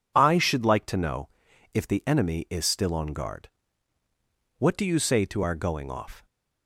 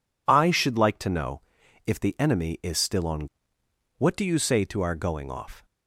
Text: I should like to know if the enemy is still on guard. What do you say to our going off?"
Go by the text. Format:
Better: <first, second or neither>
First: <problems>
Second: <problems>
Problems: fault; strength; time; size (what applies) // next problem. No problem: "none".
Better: first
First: pauses between "know" and "if"; at 1.2 s; 0.44 s long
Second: pauses between "know" and "if"; at 1.4 s; 0.44 s long // skips "guard"; at 3.6 s